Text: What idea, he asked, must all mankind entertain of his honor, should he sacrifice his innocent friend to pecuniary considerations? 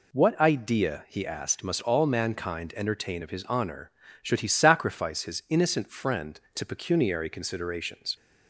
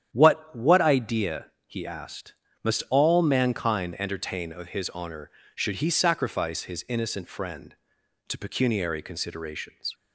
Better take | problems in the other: first | starts louder than the rest; strong; until 1.1 s; 9.5 dB // says "What" twice; at 0.5 s

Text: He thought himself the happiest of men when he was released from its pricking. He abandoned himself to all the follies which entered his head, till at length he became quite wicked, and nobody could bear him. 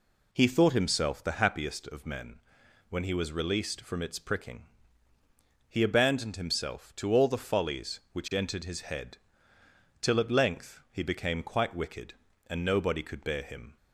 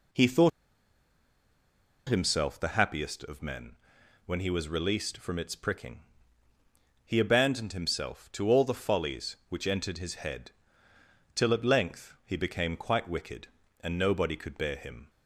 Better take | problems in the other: first | pauses between "thought" and "himself"; strong; at 0.5 s; 1.5 s long // pauses between "men" and "when"; noticeable; at 3.7 s; 0.50 s long; noticeable in the first

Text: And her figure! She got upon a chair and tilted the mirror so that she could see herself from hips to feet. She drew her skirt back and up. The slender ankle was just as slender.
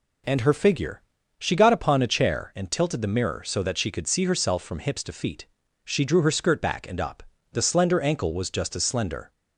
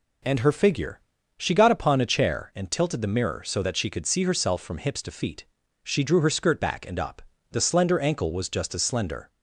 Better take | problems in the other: neither | none

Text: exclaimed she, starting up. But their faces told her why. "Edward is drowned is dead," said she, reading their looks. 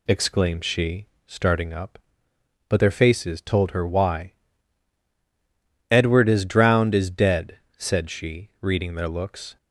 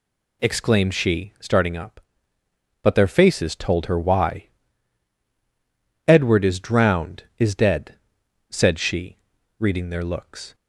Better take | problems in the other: neither | none

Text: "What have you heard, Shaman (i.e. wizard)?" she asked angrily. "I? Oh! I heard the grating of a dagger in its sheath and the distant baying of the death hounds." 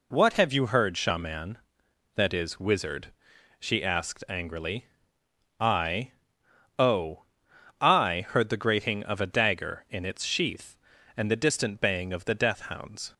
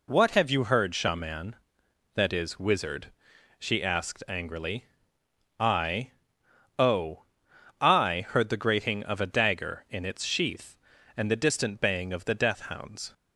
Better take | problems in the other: neither | none

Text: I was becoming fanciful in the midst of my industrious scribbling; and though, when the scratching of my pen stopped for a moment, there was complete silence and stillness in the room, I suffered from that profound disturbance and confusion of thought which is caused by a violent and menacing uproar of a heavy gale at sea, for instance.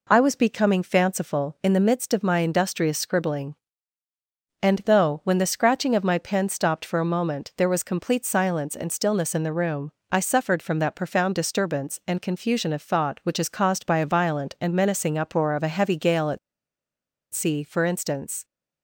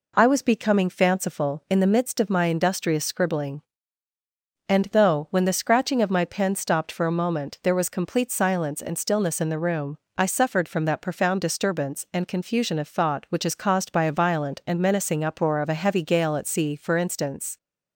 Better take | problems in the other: second | pauses between "at" and "sea"; noticeable; at 16.3 s; 0.93 s long

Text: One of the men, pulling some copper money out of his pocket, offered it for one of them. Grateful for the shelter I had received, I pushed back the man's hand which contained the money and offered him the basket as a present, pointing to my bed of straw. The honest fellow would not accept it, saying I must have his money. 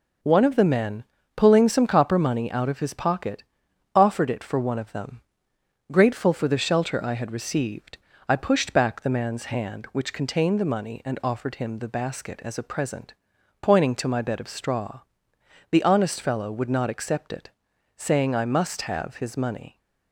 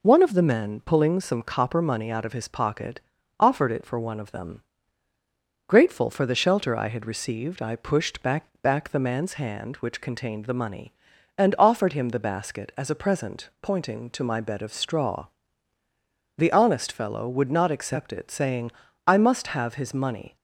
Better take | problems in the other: first | says "back" twice; at 8.6 s // pauses between "saying" and "I"; slight; at 18.7 s; 0.36 s long

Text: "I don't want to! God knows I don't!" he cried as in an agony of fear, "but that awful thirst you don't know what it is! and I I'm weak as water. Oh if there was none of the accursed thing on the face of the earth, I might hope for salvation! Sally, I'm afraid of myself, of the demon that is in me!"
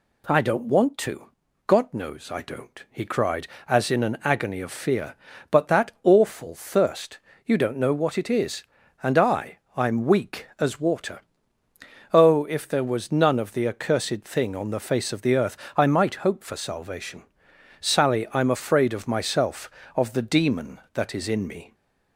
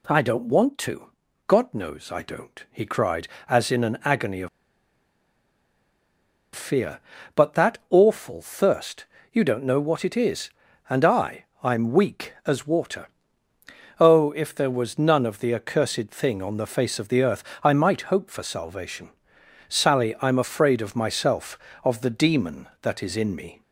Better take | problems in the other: first | pauses between "of" and "fear"; strong; at 4.4 s; 2.0 s long // pauses between "thirst" and "you"; slight; at 9.0 s; 0.28 s long; slight in the first // pauses between "I" and "I'm"; slight; at 11.4 s; 0.18 s long; slight in the first

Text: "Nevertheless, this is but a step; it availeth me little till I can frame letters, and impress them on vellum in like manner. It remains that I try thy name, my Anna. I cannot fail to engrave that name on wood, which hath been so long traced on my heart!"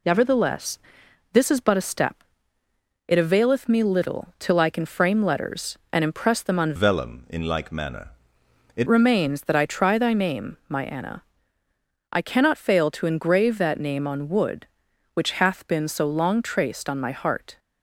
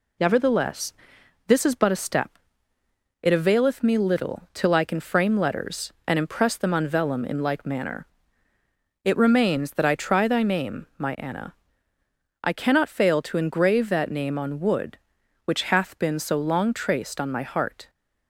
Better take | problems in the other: second | changes voice from "vellum" to "It"; from 6.7 to 8.8 s; 2.1 s long

